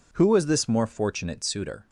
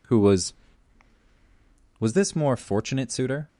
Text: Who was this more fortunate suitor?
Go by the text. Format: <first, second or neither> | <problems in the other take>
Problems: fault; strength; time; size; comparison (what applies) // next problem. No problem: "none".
first | says "was" twice; at 1.9 s